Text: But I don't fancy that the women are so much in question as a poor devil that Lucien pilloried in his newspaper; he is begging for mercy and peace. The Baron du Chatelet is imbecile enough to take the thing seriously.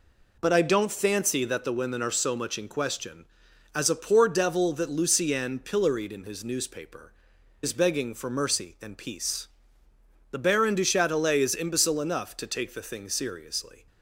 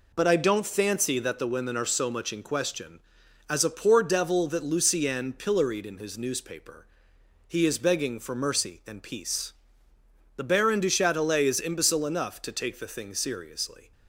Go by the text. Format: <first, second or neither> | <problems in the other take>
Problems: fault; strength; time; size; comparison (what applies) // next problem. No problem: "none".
second | skips "he"; at 7.3 s